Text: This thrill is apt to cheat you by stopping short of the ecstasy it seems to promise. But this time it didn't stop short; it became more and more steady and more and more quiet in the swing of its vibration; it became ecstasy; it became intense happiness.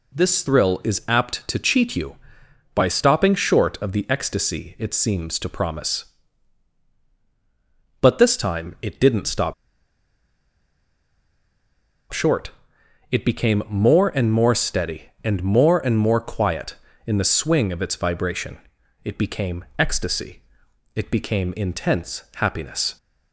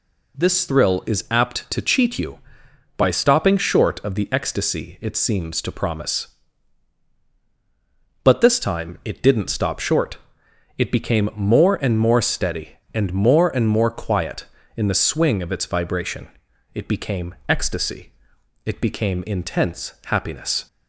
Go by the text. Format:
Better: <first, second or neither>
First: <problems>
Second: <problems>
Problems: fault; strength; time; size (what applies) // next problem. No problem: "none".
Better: second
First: pauses between "stop" and "short"; strong; at 9.5 s; 2.5 s long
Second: none